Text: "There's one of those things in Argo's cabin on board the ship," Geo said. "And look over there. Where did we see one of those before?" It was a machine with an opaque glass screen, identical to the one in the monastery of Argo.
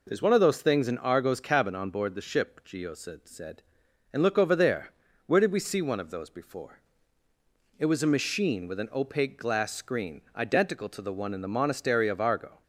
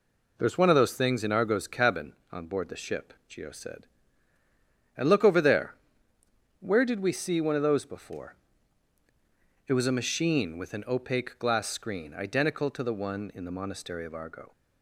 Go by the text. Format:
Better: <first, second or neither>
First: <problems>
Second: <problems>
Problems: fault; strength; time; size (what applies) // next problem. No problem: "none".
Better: second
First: says "said" twice; at 3.2 s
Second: none